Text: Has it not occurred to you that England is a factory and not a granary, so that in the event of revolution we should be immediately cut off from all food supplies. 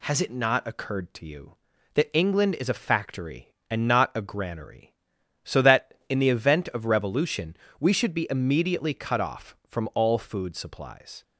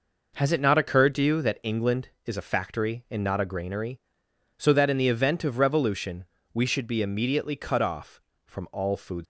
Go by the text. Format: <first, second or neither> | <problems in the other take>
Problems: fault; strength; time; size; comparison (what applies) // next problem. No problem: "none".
first | pauses between "revolution" and "we"; slight; at 6.2 s; 0.28 s long; slight in the first // stops before "supplies"; at 9.2 s